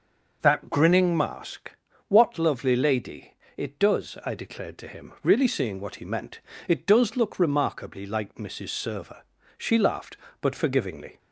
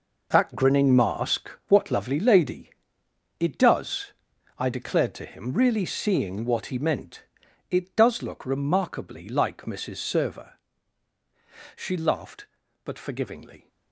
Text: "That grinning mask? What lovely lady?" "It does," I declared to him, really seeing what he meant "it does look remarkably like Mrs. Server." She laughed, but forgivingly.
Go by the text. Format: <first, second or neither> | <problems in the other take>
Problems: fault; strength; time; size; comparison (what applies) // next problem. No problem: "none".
first | gets quieter; strong; throughout; 11 dB // pauses between "meant" and "it"; noticeable; at 7.2 s; 0.48 s long; slight in the first